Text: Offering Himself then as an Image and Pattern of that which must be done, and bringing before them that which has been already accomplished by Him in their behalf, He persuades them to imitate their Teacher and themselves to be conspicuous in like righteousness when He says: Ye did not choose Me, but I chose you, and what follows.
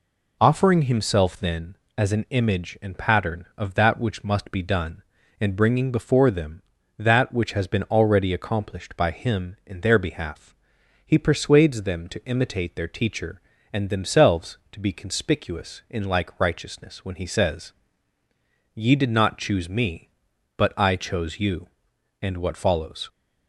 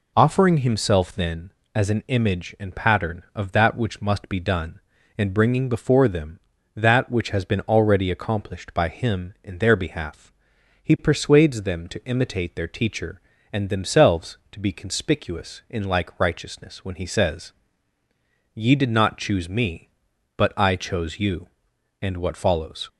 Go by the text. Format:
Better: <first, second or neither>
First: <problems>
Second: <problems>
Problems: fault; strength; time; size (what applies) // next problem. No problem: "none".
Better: neither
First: none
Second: none